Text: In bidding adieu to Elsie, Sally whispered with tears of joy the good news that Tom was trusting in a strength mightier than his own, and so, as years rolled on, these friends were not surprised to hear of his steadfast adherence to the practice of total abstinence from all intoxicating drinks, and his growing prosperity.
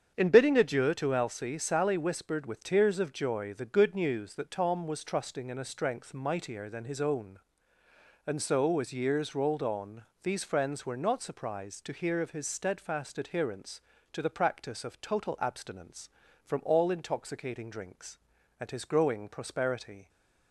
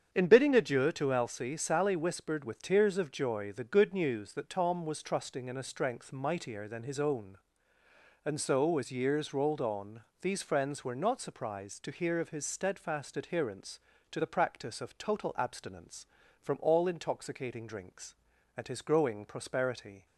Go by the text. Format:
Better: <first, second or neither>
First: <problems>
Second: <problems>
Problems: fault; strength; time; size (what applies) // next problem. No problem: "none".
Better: neither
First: starts louder than the rest; strong; until 1.1 s; 7.5 dB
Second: starts louder than the rest; strong; until 1.1 s; 7.5 dB